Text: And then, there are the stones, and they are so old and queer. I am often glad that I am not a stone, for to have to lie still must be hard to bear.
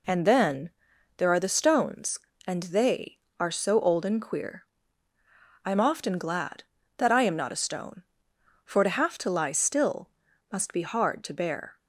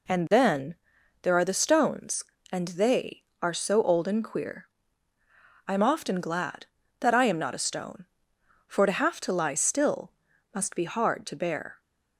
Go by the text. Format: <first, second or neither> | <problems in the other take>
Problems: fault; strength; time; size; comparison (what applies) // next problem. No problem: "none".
neither | pauses between "still" and "must"; the same in both